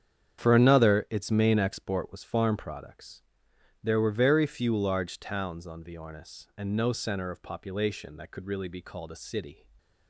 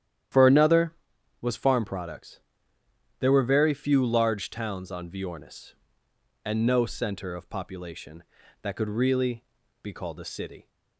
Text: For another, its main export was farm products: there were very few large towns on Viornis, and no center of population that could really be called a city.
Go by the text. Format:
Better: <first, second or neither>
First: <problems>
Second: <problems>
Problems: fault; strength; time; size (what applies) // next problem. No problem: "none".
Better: first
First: starts louder than the rest; strong; until 1.4 s; 8.5 dB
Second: starts louder than the rest; strong; until 1.8 s; 10.5 dB // skips "its main export"; at 1.1 s // pauses between "really" and "be"; at 9.4 s; 0.40 s long